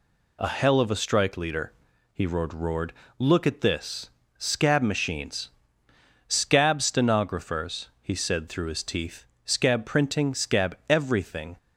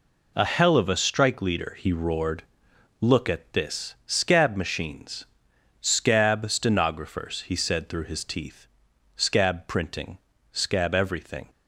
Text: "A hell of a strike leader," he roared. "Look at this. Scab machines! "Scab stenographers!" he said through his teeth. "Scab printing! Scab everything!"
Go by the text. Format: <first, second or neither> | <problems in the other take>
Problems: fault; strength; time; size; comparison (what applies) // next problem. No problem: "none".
second | says "roared" twice; at 2.5 s